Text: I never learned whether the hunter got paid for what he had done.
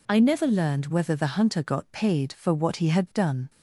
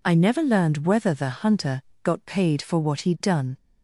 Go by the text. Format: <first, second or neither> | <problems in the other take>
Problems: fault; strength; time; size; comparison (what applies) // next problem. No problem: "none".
first | pauses between "hunter" and "got"; slight; at 1.8 s; 0.24 s long // skips "had"; at 3.1 s